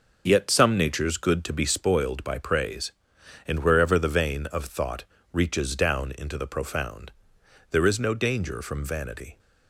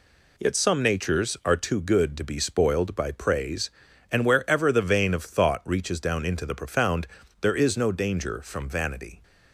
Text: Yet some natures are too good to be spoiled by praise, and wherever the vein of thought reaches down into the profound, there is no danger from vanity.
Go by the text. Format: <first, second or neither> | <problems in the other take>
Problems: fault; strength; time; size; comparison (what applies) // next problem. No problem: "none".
second | starts louder than the rest; noticeable; until 1.2 s; 6 dB // skips "are too"; at 1.1 s // pauses between "thought" and "reaches"; slight; at 5.0 s; 0.28 s long